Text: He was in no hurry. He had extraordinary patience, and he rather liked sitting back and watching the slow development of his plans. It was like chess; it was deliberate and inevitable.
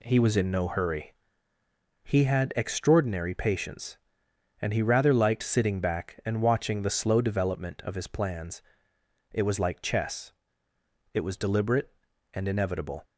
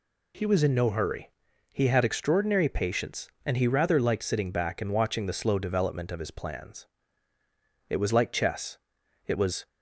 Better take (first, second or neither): first